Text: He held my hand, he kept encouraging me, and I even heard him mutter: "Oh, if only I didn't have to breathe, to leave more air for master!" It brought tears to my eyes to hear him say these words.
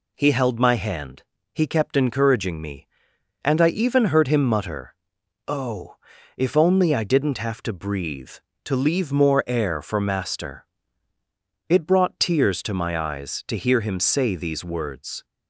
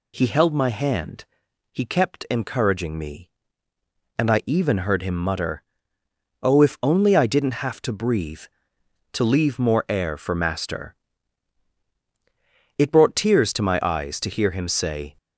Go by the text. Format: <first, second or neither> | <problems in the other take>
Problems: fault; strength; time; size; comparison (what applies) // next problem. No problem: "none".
first | stops before "these words"; at 15.1 s